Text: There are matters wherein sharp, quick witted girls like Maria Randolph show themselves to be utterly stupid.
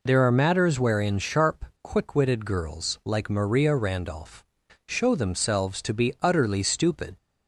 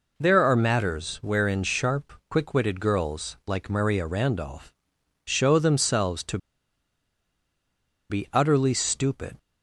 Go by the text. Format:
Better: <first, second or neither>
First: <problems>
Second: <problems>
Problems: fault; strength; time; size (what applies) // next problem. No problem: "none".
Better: first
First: pauses between "Randolph" and "show"; at 4.4 s; 0.42 s long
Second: pauses between "Randolph" and "show"; noticeable; at 4.7 s; 0.54 s long // pauses between "to" and "be"; strong; at 6.3 s; 1.7 s long